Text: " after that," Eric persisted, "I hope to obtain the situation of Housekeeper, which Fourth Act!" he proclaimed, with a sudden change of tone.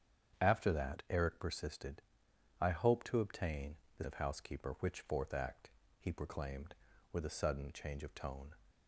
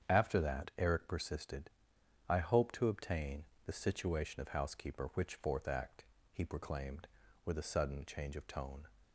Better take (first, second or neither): second